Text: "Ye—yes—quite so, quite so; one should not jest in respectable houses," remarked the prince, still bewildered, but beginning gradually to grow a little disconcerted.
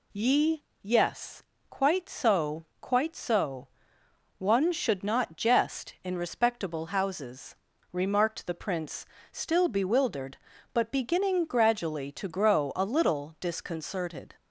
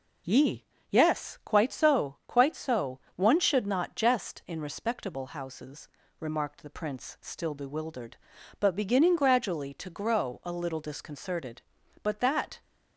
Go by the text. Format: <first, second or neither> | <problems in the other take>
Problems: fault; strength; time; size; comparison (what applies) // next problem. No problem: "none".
first | goes on to say "But that"; from 12.0 s on; 0.58 s long